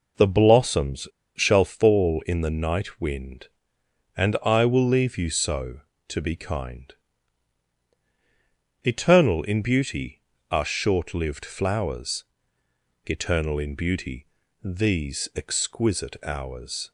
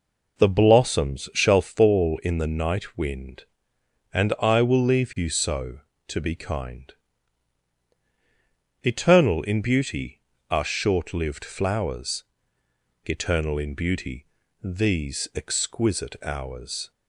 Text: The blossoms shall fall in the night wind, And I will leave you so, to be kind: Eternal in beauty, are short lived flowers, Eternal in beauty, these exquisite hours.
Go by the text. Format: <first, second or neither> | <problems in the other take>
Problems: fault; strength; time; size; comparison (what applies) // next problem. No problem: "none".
second | pauses between "blossoms" and "shall"; slight; at 1.0 s; 0.28 s long